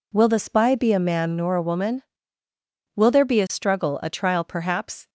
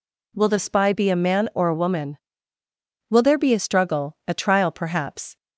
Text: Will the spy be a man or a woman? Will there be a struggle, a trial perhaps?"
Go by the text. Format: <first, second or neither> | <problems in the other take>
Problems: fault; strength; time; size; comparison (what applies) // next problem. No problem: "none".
second | says "nor" for "or"; at 1.3 s